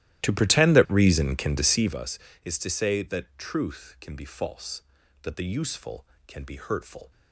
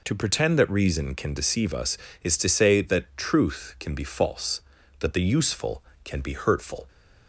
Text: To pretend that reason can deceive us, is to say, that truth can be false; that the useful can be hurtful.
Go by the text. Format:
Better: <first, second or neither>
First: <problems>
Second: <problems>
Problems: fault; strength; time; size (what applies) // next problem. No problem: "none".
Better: second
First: starts louder than the rest; strong; until 2.1 s; 14 dB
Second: none